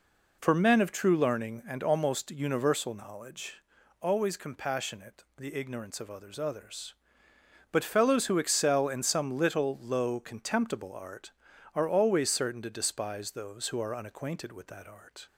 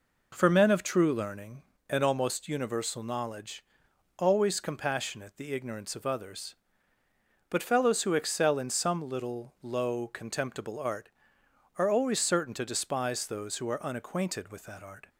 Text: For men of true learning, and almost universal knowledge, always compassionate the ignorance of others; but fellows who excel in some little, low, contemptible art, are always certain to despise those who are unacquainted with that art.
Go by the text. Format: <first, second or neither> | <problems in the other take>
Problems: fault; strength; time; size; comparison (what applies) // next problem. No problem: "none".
second | says "others" twice; at 6.3 s